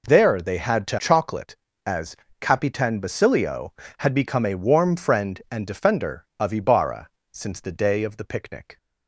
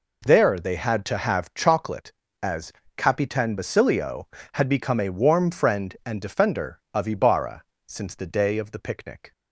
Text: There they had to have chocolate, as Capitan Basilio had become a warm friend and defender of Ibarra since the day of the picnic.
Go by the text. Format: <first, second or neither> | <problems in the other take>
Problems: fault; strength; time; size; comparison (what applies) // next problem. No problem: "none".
second | skips "have"; at 0.9 s // pauses between "as" and "Capitan"; slight; at 2.1 s; 0.24 s long; slight in the second // pauses between "Ibarra" and "since"; slight; at 7.0 s; 0.24 s long; slight in the second